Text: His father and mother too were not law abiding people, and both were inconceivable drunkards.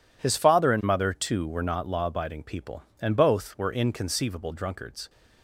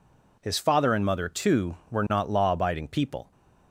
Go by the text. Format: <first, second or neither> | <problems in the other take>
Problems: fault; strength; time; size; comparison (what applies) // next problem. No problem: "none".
first | stops before "and both were inconceivable drunkards"; at 3.3 s